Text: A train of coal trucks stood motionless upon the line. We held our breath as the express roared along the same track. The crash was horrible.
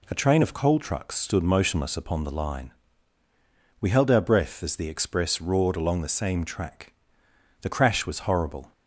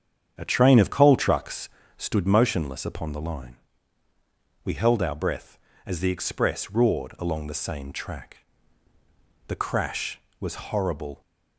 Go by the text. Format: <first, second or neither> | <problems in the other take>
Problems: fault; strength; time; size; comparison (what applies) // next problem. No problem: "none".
first | starts louder than the rest; strong; until 2.3 s; 8 dB // pauses between "trucks" and "stood"; slight; at 1.6 s; 0.30 s long